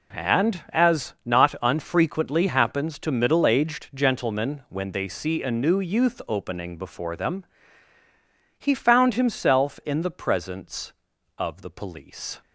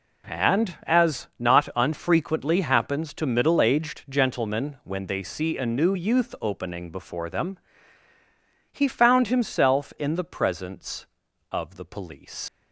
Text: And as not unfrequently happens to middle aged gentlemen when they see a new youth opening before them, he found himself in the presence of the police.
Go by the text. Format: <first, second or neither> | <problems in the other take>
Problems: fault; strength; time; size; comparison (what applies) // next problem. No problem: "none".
first | leaves "police" unfinished; at 12.4 s; 75 ms